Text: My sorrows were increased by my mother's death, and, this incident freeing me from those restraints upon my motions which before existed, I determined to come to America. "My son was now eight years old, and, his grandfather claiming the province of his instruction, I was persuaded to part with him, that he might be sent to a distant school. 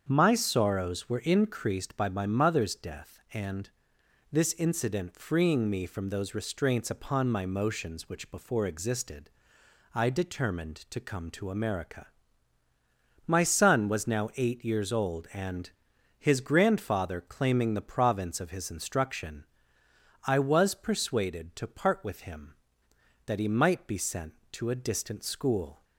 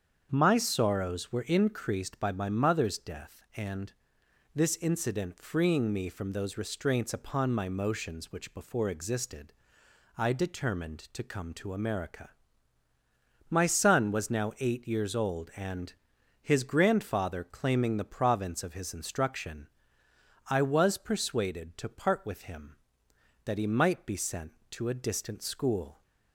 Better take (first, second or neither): neither